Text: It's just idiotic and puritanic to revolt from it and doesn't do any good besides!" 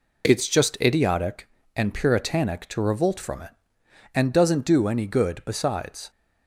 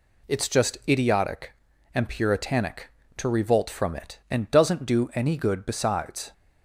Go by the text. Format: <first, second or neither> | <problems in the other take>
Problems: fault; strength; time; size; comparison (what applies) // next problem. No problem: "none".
neither | none